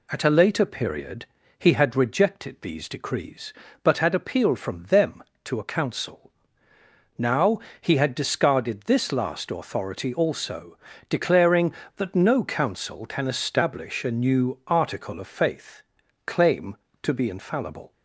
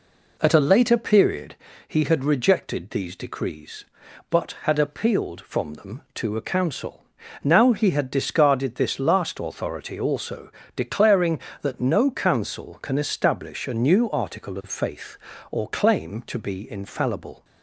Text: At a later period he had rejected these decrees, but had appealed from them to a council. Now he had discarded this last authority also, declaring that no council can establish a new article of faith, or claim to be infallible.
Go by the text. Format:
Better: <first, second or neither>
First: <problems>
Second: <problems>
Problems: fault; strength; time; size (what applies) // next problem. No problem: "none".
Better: second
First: pauses between "period" and "he"; slight; at 1.2 s; 0.32 s long // pauses between "Now" and "he"; slight; at 7.5 s; 0.22 s long // skips "or"; at 16.0 s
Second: pauses between "period" and "he"; slight; at 1.5 s; 0.32 s long